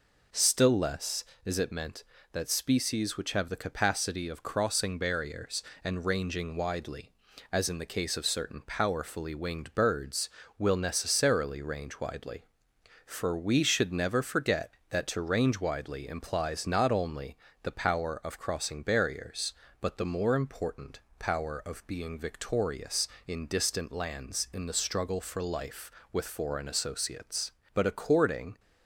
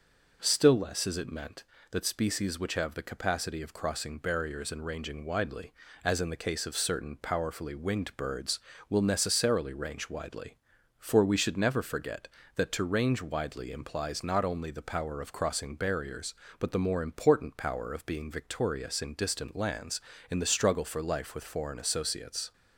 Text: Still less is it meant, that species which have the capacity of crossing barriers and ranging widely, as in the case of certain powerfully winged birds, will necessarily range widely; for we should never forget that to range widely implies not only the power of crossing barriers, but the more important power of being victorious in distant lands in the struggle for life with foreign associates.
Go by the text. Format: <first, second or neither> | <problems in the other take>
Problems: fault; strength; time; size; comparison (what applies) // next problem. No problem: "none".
second | pauses between "only" and "the"; slight; at 17.3 s; 0.28 s long // pauses between "important" and "power"; slight; at 20.9 s; 0.18 s long // goes on to say "But according"; noticeable; from 27.7 s on; 0.86 s long